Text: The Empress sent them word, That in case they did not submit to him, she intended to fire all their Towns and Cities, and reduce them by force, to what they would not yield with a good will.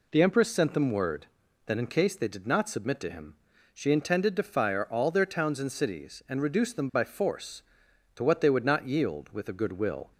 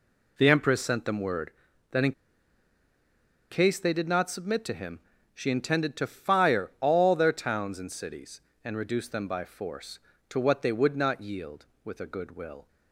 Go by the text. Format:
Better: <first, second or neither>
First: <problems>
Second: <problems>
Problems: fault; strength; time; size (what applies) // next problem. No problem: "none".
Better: first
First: none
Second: pauses between "in" and "case"; strong; at 2.1 s; 1.3 s long